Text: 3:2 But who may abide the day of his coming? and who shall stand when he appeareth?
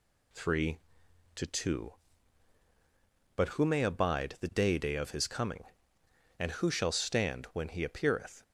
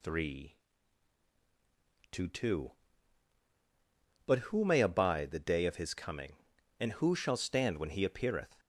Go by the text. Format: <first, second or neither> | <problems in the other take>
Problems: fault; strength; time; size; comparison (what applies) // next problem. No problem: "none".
second | says "day" twice; at 4.7 s